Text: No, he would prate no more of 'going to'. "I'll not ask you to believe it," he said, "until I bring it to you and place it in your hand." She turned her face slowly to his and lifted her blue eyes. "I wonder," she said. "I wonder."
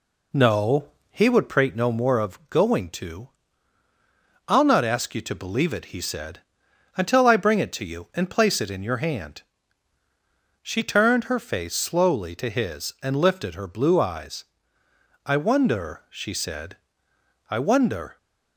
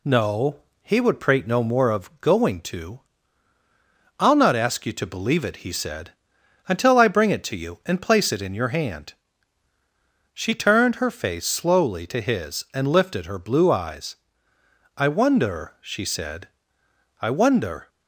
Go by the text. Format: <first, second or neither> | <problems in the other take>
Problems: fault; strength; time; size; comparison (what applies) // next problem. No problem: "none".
second | starts louder than the rest; slight; until 1.6 s; 2.5 dB